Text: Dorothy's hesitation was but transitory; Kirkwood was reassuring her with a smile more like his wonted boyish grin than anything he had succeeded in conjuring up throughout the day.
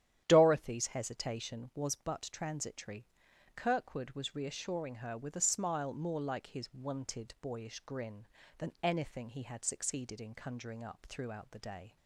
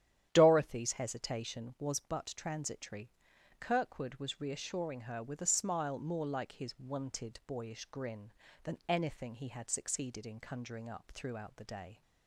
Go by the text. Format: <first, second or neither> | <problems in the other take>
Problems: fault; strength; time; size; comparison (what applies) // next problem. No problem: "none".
neither | starts louder than the rest; strong; the same in both